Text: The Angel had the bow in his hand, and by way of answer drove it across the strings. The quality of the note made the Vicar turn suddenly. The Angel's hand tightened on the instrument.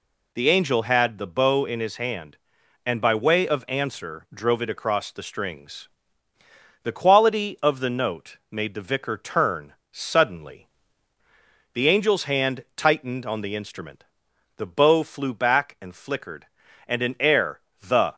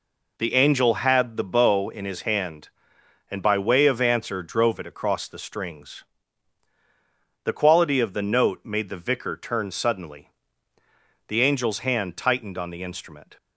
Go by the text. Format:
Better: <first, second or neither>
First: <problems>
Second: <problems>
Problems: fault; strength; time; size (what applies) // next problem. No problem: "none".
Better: second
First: pauses between "turn" and "suddenly"; slight; at 9.7 s; 0.18 s long // goes on to say "The bow flew back and flickered and an air the"; strong; from 14.5 s on; 3.5 s long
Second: none